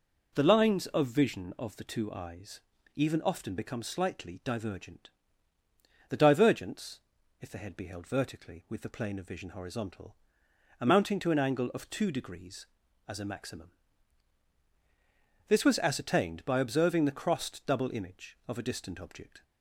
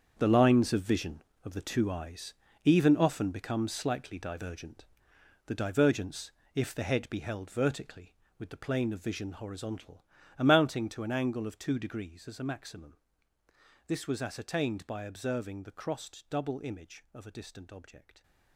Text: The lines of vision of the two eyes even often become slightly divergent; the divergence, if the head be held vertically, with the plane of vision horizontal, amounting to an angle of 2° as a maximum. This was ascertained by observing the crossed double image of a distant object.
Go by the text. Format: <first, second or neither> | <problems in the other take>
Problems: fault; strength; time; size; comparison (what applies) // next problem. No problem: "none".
first | gets quieter; strong; throughout; 13 dB // pauses between "eyes" and "even"; slight; at 2.3 s; 0.32 s long; slight in the first